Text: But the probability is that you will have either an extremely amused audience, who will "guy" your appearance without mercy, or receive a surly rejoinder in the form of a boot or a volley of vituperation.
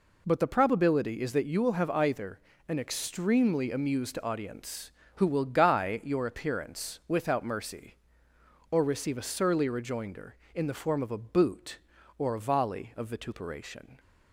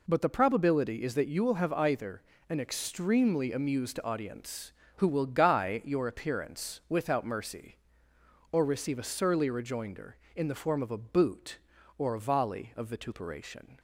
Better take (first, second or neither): neither